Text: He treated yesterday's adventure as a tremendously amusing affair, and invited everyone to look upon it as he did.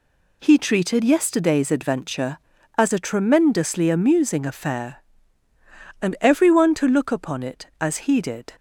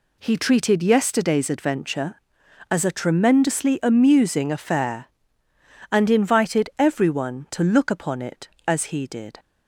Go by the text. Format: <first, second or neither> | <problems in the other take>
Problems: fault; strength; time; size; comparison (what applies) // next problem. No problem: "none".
second | skips "invited"; at 6.1 s